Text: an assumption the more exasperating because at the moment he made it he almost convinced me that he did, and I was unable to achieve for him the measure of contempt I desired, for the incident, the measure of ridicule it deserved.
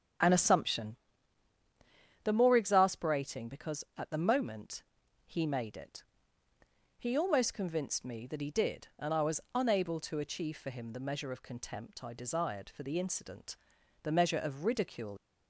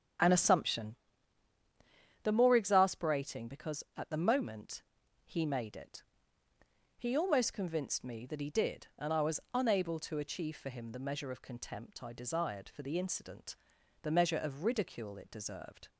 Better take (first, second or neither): second